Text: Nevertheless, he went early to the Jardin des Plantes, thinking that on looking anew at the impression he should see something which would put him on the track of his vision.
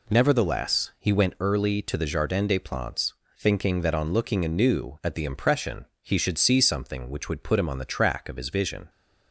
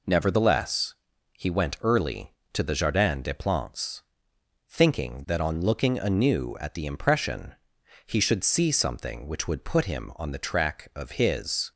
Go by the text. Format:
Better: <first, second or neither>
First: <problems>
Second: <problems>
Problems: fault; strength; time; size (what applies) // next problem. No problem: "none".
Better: first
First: pauses between "impression" and "he"; slight; at 5.8 s; 0.16 s long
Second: pauses between "impression" and "he"; noticeable; at 7.5 s; 0.52 s long // stops before "vision"; at 11.7 s